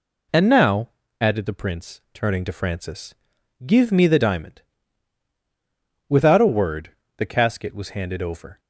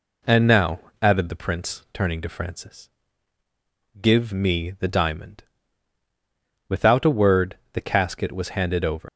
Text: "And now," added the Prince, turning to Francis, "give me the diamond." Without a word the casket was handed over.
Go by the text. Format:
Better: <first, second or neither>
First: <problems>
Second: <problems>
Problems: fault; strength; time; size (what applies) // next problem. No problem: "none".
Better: first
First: pauses between "word" and "the"; slight; at 6.9 s; 0.26 s long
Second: pauses between "word" and "the"; slight; at 7.5 s; 0.16 s long // leaves "over" unfinished; at 9.0 s; 85 ms